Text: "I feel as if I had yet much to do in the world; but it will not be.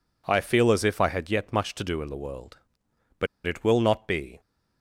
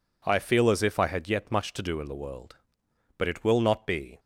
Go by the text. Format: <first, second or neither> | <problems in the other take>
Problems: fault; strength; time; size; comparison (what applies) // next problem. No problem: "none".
second | pauses between "but" and "it"; slight; at 3.2 s; 0.19 s long